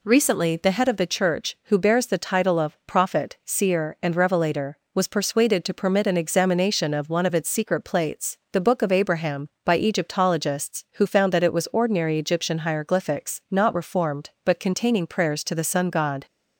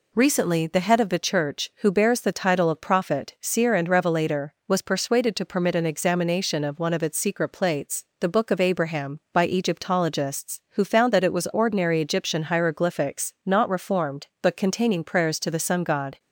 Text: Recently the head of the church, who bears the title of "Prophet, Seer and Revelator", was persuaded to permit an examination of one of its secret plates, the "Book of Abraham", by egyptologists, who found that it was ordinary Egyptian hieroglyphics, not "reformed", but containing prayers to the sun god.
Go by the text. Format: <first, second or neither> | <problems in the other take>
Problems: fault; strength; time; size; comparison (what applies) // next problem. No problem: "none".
neither | none